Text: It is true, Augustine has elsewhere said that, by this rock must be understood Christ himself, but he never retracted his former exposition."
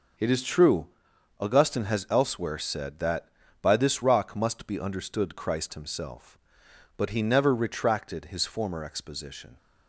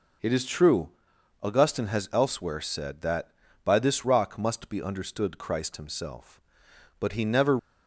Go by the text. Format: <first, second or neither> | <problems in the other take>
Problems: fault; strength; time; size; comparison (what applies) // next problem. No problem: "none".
first | stops before "retracted his former exposition"; at 7.5 s